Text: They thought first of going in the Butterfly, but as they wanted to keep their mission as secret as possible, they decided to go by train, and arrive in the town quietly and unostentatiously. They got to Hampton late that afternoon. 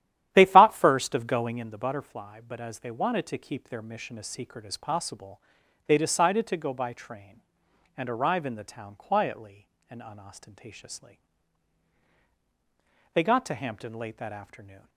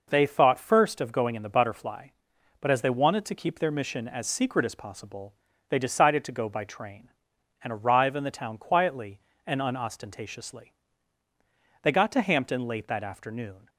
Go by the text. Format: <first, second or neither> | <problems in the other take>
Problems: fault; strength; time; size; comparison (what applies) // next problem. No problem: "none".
second | starts louder than the rest; strong; until 1.7 s; 12 dB